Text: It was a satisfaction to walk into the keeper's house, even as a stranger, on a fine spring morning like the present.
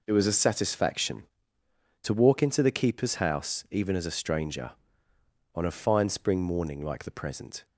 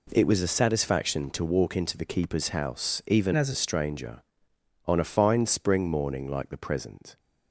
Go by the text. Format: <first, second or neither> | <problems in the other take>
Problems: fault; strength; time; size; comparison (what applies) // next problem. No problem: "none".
first | changes voice from "as" to "a"; from 3.3 to 3.5 s; 0.2 s long